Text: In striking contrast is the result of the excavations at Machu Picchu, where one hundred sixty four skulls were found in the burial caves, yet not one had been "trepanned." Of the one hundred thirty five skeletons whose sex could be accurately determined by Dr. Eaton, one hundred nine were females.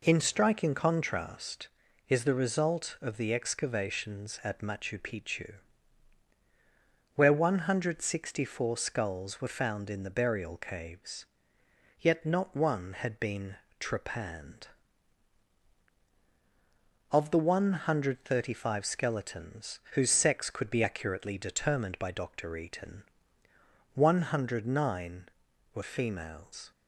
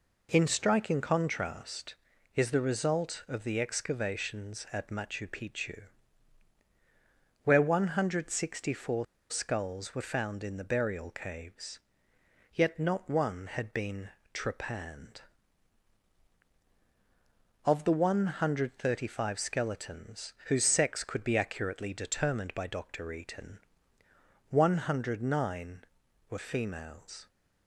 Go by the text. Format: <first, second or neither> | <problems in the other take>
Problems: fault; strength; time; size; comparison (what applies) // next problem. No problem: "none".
first | pauses between "four" and "skulls"; slight; at 9.0 s; 0.25 s long // pauses between "been" and "trepanned"; slight; at 14.1 s; 0.22 s long; slight in the first